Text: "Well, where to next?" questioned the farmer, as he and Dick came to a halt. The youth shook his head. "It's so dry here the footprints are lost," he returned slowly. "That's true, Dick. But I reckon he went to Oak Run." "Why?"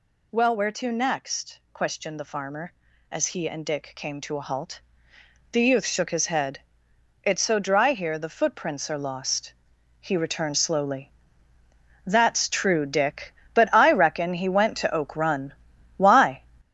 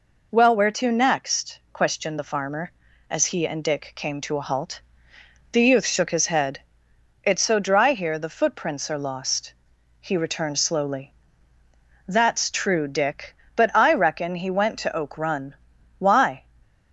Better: second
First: gets louder; noticeable; throughout; 5.5 dB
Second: none

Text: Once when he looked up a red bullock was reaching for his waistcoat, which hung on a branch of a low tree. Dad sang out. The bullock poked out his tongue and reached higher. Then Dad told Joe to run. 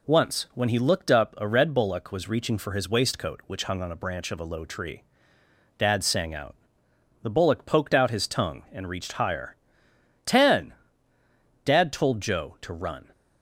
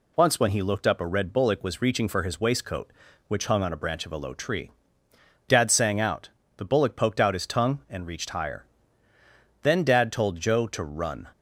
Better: second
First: says "Ten" for "Then"; at 10.2 s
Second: none

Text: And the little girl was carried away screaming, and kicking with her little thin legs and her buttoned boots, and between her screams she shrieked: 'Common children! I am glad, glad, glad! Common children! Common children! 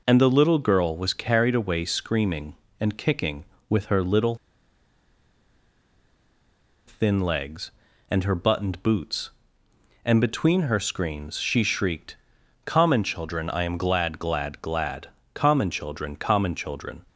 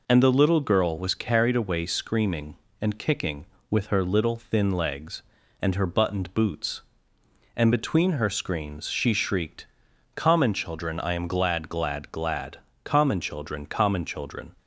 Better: second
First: pauses between "little" and "thin"; strong; at 4.3 s; 2.5 s long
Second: none

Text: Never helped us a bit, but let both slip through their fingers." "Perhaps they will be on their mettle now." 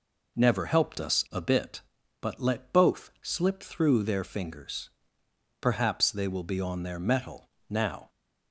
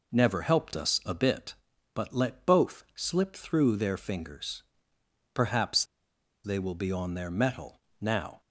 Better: first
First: pauses between "mettle" and "now"; slight; at 7.5 s; 0.18 s long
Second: pauses between "Perhaps" and "they"; noticeable; at 5.8 s; 0.60 s long // pauses between "mettle" and "now"; slight; at 7.8 s; 0.18 s long

